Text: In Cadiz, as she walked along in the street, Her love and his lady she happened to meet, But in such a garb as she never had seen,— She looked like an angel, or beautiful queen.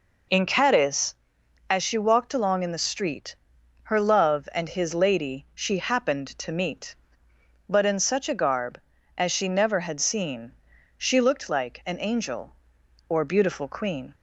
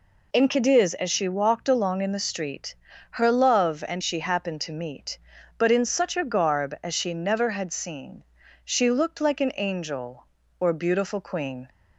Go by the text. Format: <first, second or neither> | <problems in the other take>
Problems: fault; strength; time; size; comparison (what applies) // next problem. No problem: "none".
first | skips "his lady"; at 4.0 s